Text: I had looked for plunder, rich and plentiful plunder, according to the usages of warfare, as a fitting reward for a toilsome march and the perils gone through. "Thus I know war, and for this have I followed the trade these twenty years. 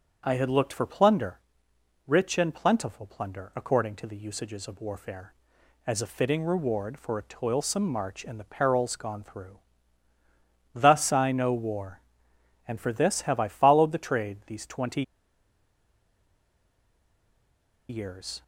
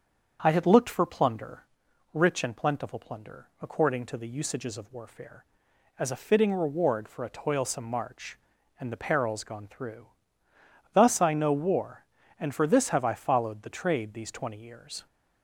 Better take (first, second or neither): second